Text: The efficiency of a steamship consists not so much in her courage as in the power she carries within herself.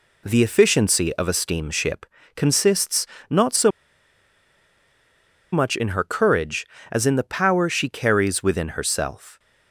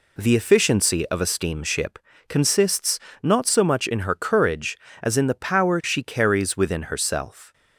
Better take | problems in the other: second | pauses between "steamship" and "consists"; slight; at 2.0 s; 0.30 s long; slight in the second // pauses between "consists" and "not"; slight; at 3.0 s; 0.24 s long; slight in the second // pauses between "so" and "much"; strong; at 3.6 s; 1.8 s long

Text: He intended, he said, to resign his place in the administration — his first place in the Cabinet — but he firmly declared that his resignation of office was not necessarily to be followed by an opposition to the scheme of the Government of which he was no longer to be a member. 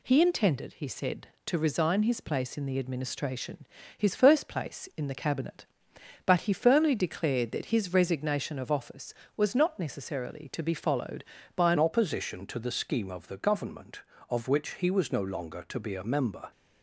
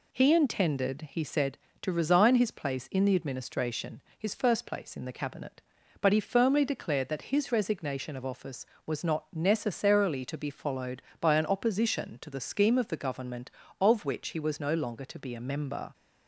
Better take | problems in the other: second | changes voice at "opposition"; from 11.7 s on; 4.8 s long

